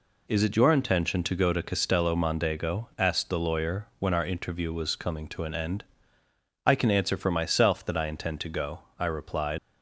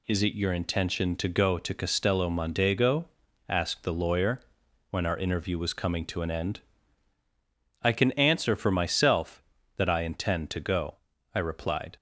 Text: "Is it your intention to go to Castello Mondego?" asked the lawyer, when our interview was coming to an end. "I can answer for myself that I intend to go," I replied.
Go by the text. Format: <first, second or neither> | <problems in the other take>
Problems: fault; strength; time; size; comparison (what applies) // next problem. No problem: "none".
second | leaves "replied" unfinished; at 9.5 s; 100 ms